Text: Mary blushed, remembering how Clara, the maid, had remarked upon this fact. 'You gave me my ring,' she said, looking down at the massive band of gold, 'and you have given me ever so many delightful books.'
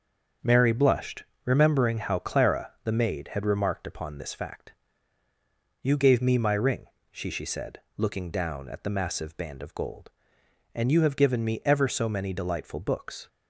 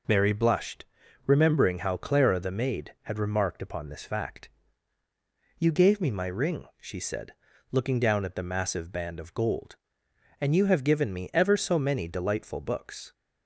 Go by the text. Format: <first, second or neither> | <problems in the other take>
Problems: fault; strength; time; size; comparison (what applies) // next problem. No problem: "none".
second | starts louder than the rest; until 1.6 s; 6.5 dB // says "she" twice; at 7.2 s